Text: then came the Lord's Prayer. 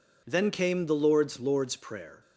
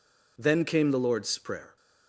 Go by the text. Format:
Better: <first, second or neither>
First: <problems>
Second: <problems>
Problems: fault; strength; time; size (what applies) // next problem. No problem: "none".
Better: second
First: says "Lord's" twice; at 1.3 s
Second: none